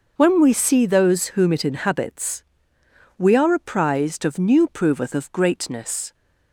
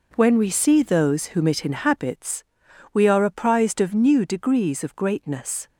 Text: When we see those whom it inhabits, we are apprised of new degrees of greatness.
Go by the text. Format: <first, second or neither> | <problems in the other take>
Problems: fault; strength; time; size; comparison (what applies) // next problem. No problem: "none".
second | says "proveth" for "degrees"; at 4.6 s